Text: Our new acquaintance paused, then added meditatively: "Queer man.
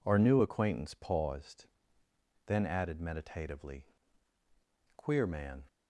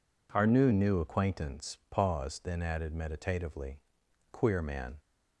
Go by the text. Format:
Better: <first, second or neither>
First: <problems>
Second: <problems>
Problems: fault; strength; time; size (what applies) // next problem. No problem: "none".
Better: first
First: none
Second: says "new" twice; at 0.7 s